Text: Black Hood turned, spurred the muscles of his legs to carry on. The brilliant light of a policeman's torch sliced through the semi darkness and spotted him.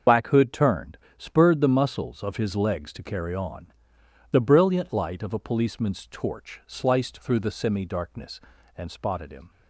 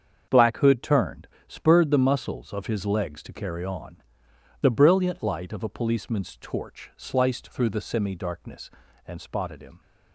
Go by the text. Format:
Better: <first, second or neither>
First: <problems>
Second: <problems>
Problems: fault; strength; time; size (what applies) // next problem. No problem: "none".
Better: second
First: loses the start of "Black"; at 0.0 s; 70 ms // starts louder than the rest; until 1.2 s; 6.5 dB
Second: starts louder than the rest; until 1.4 s; 7 dB